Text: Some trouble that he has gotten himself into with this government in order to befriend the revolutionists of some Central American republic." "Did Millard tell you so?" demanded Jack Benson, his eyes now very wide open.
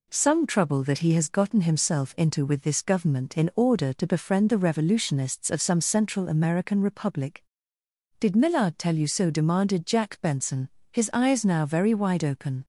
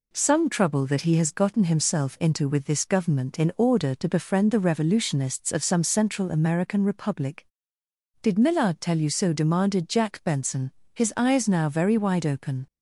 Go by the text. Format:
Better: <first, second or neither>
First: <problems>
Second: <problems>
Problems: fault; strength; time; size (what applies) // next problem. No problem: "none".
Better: neither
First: none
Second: none